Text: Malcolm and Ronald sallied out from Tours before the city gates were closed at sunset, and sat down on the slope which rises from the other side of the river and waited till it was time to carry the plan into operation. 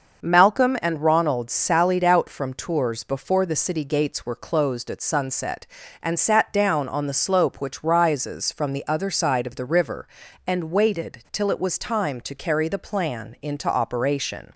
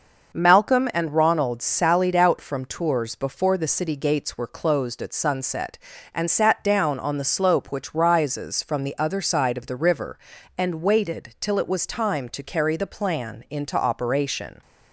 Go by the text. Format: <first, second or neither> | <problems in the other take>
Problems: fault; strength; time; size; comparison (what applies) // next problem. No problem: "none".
neither | starts louder than the rest; noticeable; the same in both